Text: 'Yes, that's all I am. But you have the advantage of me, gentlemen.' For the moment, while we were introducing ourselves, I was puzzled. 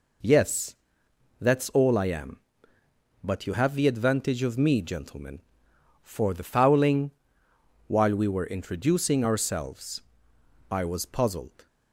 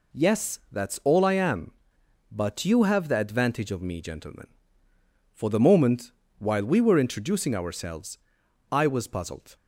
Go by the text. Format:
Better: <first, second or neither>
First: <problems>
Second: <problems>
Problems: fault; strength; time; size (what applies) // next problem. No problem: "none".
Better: second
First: says "fouling" for "moment"; at 6.4 s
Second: none